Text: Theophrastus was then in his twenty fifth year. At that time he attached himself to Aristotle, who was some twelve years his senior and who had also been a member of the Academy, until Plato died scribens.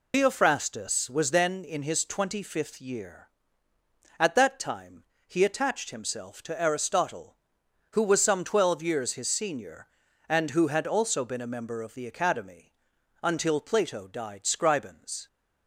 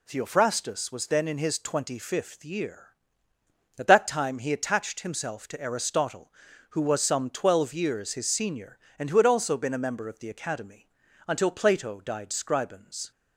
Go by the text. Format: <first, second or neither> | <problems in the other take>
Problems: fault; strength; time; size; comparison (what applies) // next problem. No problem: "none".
second | loses the start of "Theophrastus"; at 0.1 s; 155 ms // pauses between "time" and "he"; slight; at 5.0 s; 0.22 s long